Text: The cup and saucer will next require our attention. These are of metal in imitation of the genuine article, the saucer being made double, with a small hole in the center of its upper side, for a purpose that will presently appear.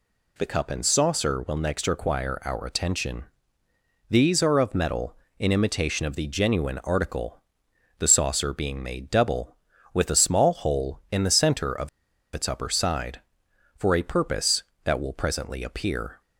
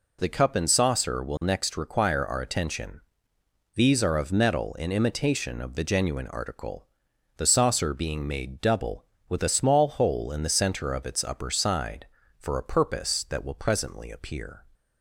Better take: second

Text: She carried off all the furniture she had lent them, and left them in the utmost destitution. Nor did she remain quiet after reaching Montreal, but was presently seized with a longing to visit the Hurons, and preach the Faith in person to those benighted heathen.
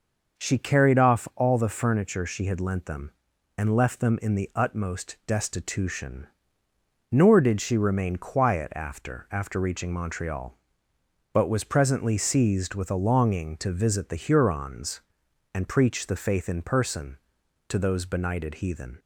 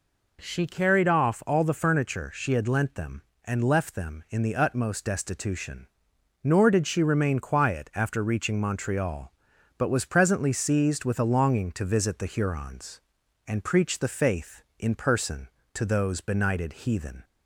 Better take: second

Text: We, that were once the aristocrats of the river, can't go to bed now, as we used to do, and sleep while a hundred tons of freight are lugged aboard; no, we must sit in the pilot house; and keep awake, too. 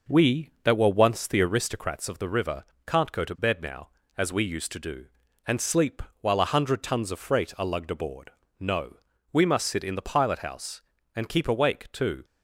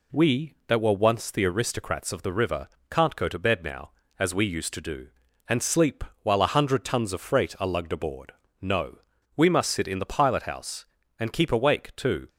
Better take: second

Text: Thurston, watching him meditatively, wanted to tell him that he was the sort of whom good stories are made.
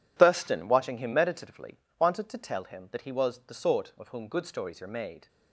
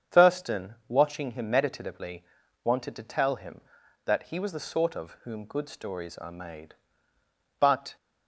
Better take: first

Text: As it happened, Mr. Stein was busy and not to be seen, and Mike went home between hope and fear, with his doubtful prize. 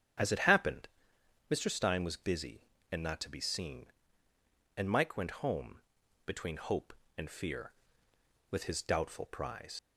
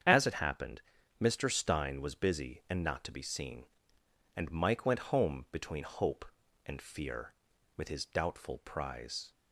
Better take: second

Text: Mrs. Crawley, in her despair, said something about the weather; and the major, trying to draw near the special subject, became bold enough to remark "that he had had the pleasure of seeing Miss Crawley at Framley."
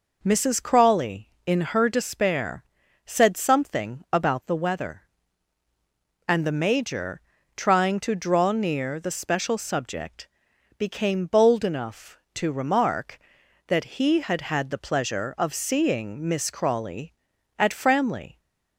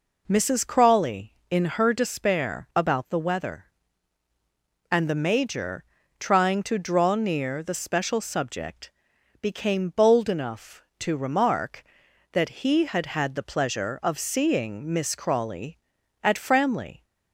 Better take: first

